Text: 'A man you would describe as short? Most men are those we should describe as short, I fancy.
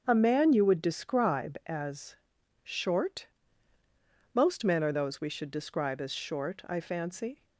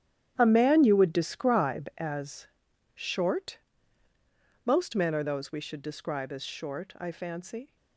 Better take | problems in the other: first | gets quieter; strong; throughout; 14.5 dB // starts louder than the rest; strong; until 1.3 s; 10.5 dB; also in the first // pauses between "as" and "short"; noticeable; at 2.4 s; 0.46 s long; noticeable in the first

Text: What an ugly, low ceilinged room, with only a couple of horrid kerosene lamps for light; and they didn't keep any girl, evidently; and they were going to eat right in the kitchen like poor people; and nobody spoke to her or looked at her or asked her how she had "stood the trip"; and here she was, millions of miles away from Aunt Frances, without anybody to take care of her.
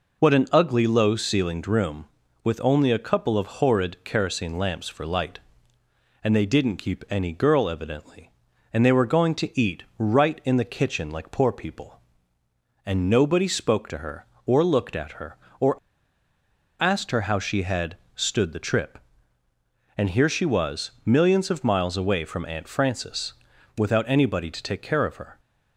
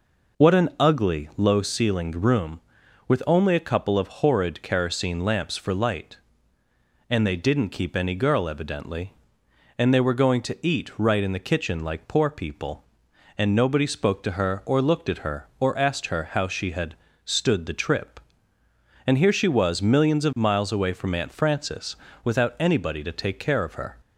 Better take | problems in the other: second | pauses between "eat" and "right"; slight; at 9.8 s; 0.16 s long // pauses between "or" and "asked"; at 15.7 s; 1.0 s long // pauses between "had" and "stood"; slight; at 17.9 s; 0.20 s long; slight in the second

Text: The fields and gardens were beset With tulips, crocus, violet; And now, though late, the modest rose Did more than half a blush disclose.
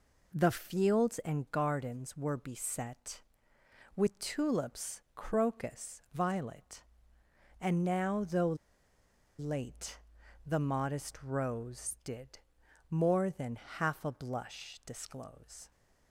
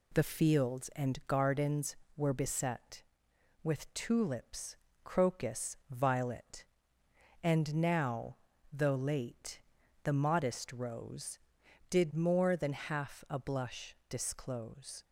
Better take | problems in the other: second | pauses between "though" and "late"; noticeable; at 8.5 s; 0.83 s long // pauses between "Did" and "more"; noticeable; at 12.4 s; 0.50 s long

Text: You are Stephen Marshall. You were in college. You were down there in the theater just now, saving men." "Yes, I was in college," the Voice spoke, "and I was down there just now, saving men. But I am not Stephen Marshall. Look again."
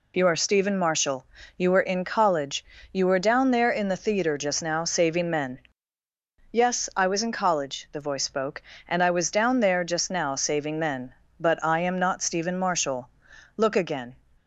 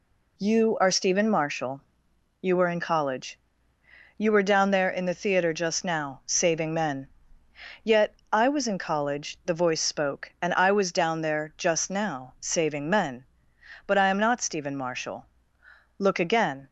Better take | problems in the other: first | says "Yet" for "Yes"; at 7.8 s

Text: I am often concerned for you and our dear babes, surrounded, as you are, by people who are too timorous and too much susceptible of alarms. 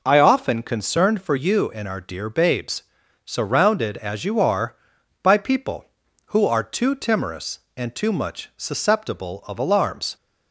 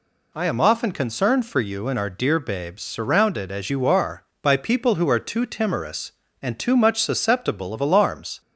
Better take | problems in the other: second | skips "am"; at 0.1 s

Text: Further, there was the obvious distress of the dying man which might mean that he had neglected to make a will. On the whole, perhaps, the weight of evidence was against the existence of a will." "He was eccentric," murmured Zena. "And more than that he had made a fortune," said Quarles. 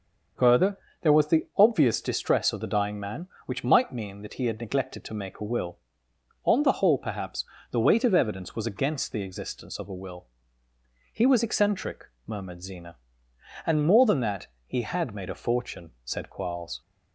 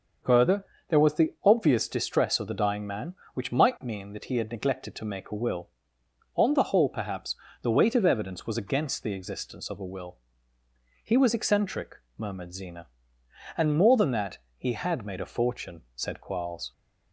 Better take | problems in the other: neither | starts louder than the rest; the same in both // pauses between "that" and "he"; slight; the same in both

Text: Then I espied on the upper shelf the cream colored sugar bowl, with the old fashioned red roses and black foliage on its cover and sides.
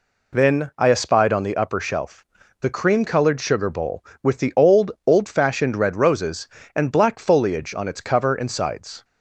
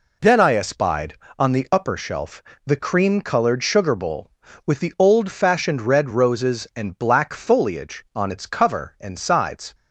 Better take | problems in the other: second | pauses between "shelf" and "the"; slight; at 2.2 s; 0.34 s long; slight in the second // says "old" twice; at 5.0 s

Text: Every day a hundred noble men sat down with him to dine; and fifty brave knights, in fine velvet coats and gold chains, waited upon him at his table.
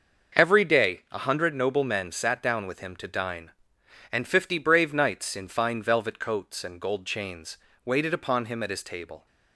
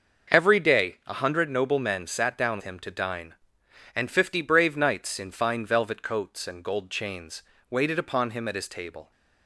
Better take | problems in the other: first | starts louder than the rest; until 1.4 s; 6 dB; also in the first // skips "with"; at 2.6 s

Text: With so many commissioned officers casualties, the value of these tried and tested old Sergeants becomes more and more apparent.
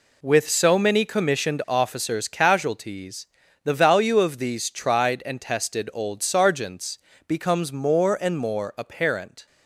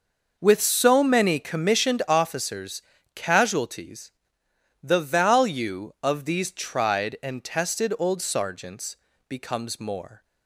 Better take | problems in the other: first | pauses between "officers" and "casualties"; slight; at 2.8 s; 0.32 s long // pauses between "Sergeants" and "becomes"; slight; at 8.9 s; 0.32 s long; slight in the first // stops before "and more apparent"; at 10.2 s

